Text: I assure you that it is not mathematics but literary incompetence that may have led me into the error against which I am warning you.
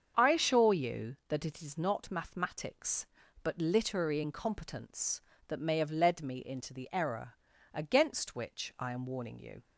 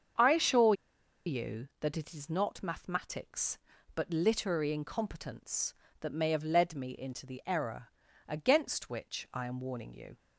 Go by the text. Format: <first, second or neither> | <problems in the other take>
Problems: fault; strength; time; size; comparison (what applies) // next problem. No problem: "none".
first | starts louder than the rest; until 1.8 s; 7 dB; also in the first // pauses between "assure" and "you"; noticeable; at 0.7 s; 0.53 s long // pauses between "error" and "against"; at 7.8 s; 0.40 s long; also in the first